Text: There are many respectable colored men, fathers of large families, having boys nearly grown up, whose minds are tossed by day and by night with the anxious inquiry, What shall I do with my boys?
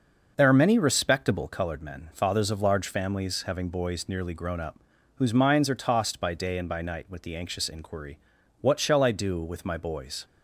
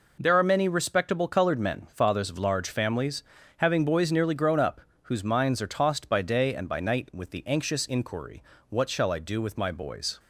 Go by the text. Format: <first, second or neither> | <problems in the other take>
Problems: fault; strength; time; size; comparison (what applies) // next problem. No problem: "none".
neither | none